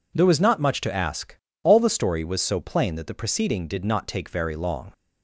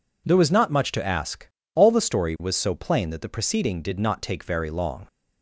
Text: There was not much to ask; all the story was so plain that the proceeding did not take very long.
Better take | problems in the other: neither | none

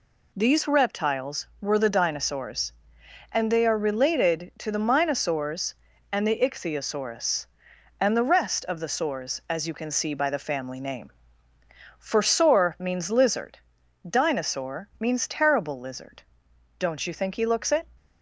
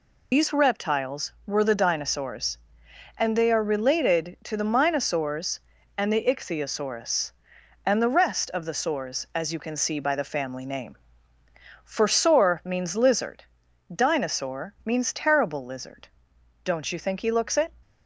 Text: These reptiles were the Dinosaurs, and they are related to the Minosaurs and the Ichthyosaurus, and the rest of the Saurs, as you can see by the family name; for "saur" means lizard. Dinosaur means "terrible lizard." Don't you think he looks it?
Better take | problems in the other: first | loses the start of "These"; at 0.3 s; 120 ms

